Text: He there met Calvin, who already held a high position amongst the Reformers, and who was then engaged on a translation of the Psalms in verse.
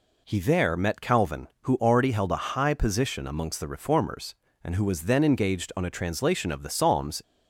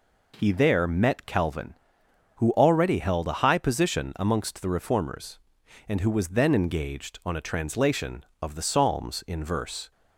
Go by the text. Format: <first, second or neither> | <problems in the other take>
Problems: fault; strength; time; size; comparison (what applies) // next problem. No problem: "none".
second | stops before "in verse"; at 7.2 s